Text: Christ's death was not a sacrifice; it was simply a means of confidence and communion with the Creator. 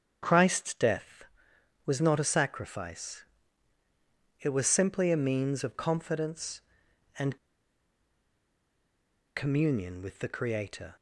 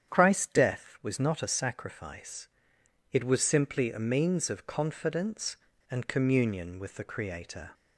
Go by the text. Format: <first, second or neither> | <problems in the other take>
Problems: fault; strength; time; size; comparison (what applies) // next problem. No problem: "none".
second | starts louder than the rest; strong; until 1.2 s; 7.5 dB; strong in the second // pauses between "and" and "communion"; strong; at 7.3 s; 2.0 s long